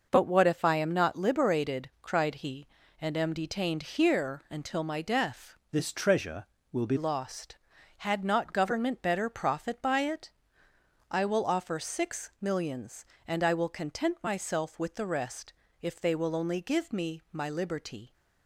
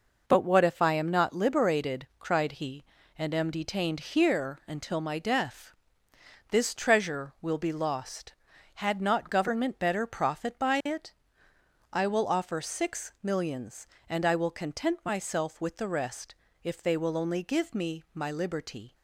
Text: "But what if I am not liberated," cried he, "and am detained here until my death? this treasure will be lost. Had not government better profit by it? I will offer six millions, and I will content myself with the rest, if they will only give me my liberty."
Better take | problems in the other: second | starts louder than the rest; noticeable; until 1.1 s; 6 dB // changes voice from "this" to "be"; from 5.7 to 6.9 s; 1.2 s long

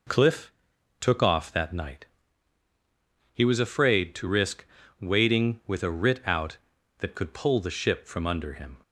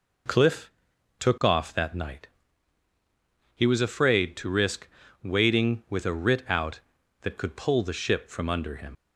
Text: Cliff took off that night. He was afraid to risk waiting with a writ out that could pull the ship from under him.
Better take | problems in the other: first | pauses between "Cliff" and "took"; noticeable; at 0.7 s; 0.48 s long; noticeable in the first // pauses between "risk" and "waiting"; slight; at 4.8 s; 0.36 s long; slight in the first // leaves "him" unfinished; at 8.9 s; 95 ms

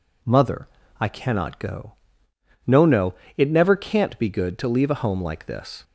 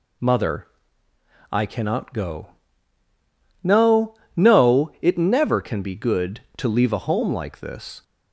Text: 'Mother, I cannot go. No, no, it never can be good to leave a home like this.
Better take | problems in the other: second | says "can't" for "can"; at 3.7 s

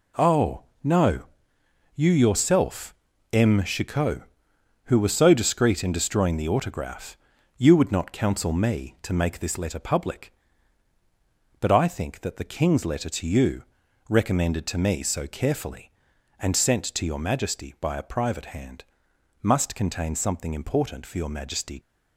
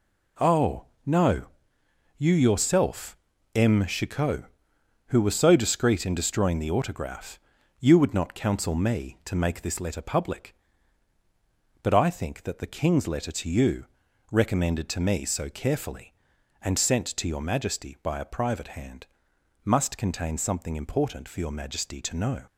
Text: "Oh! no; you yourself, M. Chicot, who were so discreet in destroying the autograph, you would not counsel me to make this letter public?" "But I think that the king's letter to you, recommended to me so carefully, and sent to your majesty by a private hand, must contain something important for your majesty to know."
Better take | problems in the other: second | stops before "to know"; at 21.7 s

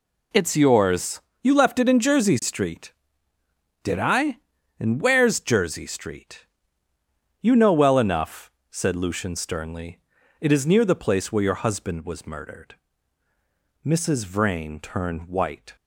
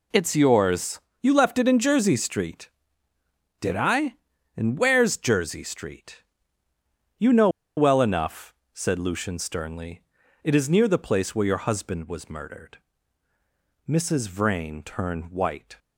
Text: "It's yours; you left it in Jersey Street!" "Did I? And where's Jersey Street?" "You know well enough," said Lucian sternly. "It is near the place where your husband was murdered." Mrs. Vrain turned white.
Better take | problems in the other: first | pauses between "know" and "well"; slight; at 7.4 s; 0.28 s long

